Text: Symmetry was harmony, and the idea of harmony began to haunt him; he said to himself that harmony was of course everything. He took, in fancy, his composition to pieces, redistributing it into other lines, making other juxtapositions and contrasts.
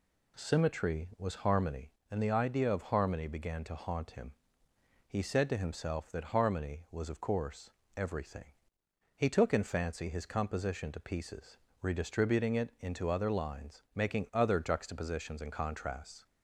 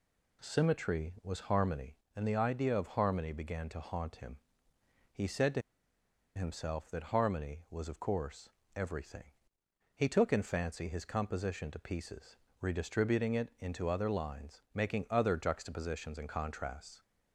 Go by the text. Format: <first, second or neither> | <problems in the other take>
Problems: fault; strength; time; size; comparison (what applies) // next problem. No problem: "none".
first | pauses between "to" and "himself"; noticeable; at 5.6 s; 0.75 s long // pauses between "course" and "everything"; slight; at 8.4 s; 0.26 s long; slight in the first